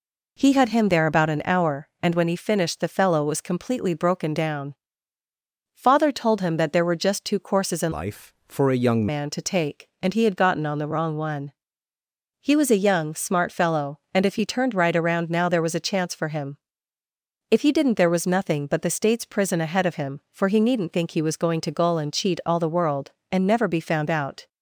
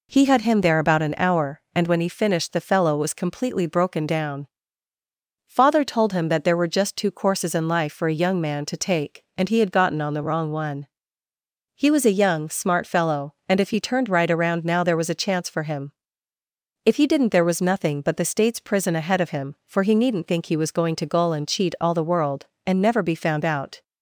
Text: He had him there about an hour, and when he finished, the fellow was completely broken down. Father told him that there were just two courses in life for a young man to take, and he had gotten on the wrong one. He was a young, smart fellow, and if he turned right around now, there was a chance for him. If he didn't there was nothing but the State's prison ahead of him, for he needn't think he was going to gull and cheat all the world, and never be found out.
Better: second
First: changes voice from "life" to "young"; from 7.9 to 9.0 s; 1.1 s long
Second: none

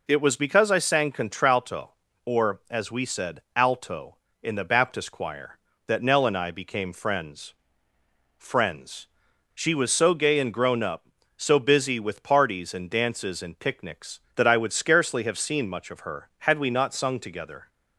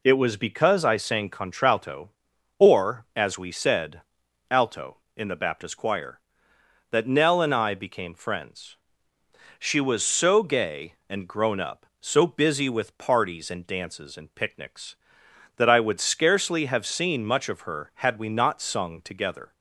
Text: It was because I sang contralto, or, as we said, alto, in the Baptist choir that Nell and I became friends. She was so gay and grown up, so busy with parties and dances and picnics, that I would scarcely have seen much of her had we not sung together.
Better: second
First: says "friends" twice; at 8.3 s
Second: none

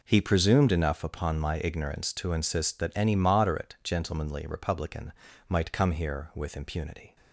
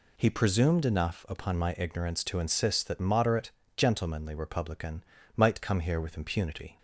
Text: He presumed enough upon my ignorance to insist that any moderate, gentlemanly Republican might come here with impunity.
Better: first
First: pauses between "Republican" and "might"; slight; at 5.1 s; 0.36 s long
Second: skips "any"; at 2.9 s // pauses between "Republican" and "might"; slight; at 5.0 s; 0.32 s long

